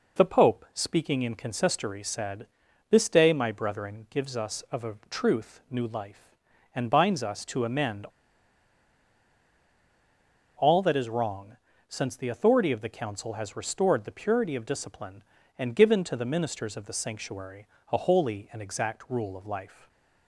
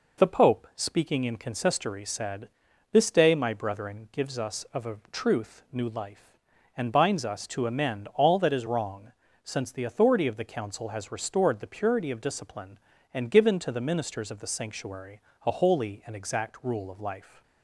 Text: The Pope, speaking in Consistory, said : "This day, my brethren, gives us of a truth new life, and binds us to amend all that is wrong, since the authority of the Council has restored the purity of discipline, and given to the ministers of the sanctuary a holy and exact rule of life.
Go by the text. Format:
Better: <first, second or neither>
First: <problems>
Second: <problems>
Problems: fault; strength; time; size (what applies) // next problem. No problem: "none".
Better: second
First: pauses between "a" and "truth"; slight; at 4.9 s; 0.16 s long // pauses between "amend" and "all"; strong; at 8.0 s; 2.5 s long // pauses between "sanctuary" and "a"; slight; at 17.6 s; 0.24 s long // stays silent after the last word; slight; from 19.6 s on; 0.6 s long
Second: pauses between "a" and "truth"; slight; at 4.9 s; 0.16 s long // pauses between "sanctuary" and "a"; slight; at 15.2 s; 0.24 s long